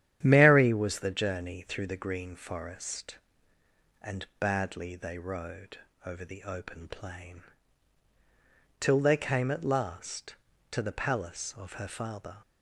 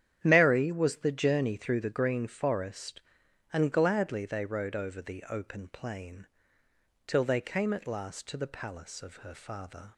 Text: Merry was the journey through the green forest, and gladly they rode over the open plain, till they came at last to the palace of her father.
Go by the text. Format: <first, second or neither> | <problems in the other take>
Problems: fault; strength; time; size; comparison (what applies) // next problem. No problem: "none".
second | starts louder than the rest; strong; until 1.2 s; 10.5 dB; strong in the second // says "badly" for "gladly"; at 4.3 s // pauses between "rode" and "over"; slight; at 5.7 s; 0.28 s long